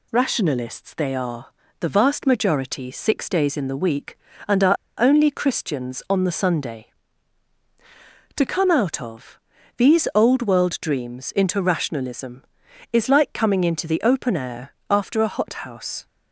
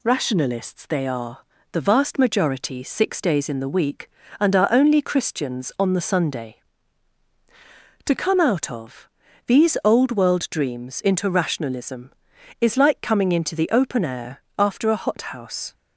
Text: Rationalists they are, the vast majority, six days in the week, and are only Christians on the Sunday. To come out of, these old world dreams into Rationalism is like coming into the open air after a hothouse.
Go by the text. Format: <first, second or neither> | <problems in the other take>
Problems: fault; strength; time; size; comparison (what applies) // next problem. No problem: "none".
second | pauses between "are" and "only"; slight; at 4.7 s; 0.25 s long // pauses between "air" and "after"; slight; at 14.7 s; 0.16 s long; slight in the second